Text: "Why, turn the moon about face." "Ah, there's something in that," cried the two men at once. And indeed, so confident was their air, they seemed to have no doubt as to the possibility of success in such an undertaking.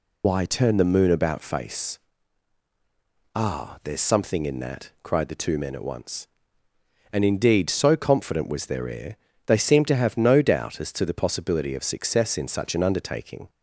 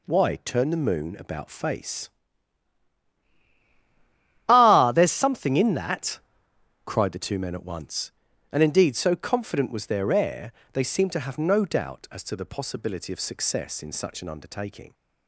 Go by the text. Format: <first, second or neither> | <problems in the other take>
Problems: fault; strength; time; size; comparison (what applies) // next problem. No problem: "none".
second | loses the start of "Why"; at 0.2 s; 75 ms